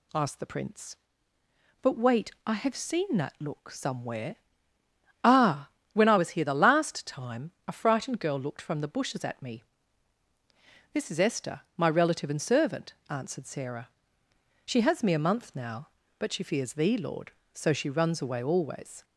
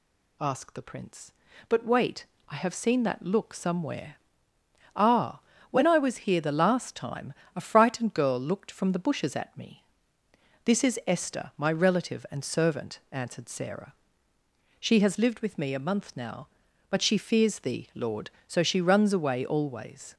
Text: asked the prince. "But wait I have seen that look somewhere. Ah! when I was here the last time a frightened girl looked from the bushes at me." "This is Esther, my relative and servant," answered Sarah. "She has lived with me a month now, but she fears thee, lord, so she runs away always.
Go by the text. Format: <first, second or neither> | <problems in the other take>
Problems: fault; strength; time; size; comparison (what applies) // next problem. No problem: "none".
second | pauses between "wait" and "I"; slight; at 2.3 s; 0.16 s long; slight in the second // pauses between "time" and "a"; slight; at 7.4 s; 0.16 s long; slight in the second // skips "lived with"; at 15.0 s